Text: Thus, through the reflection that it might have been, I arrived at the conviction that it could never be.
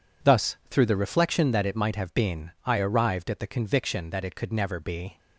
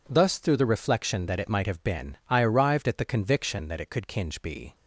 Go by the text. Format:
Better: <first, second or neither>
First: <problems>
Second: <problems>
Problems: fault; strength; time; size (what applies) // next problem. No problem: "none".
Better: first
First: none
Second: says "kinge" for "never"; at 4.0 s